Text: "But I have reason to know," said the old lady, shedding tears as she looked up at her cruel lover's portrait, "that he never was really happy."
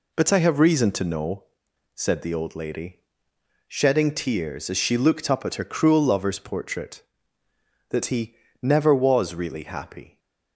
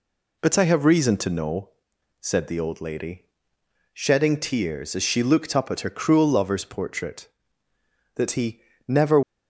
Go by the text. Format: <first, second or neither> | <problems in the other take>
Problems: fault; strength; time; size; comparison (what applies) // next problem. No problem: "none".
first | pauses between "he" and "never"; slight; at 8.6 s; 0.24 s long; slight in the first // stops before "was really happy"; at 9.2 s